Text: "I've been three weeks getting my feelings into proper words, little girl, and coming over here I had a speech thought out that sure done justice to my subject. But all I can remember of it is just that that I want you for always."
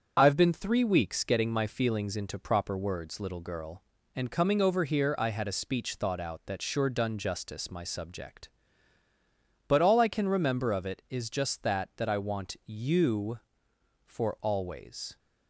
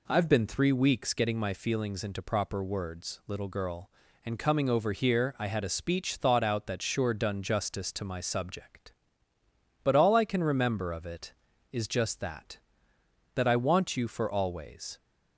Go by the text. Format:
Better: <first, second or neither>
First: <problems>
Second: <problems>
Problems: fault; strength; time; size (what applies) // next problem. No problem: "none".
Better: second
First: starts louder than the rest; until 1.1 s; 7 dB // skips "to"; at 7.7 s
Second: none